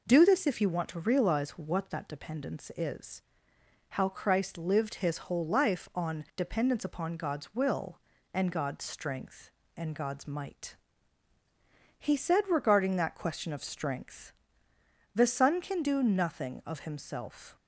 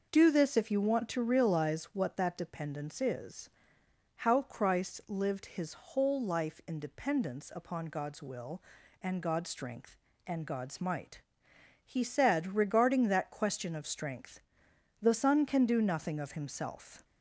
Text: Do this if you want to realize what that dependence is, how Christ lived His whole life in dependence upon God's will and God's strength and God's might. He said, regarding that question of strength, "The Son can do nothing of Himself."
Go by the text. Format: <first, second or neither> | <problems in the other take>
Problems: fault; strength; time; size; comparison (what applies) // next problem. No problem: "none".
second | says "on" for "in"; at 5.9 s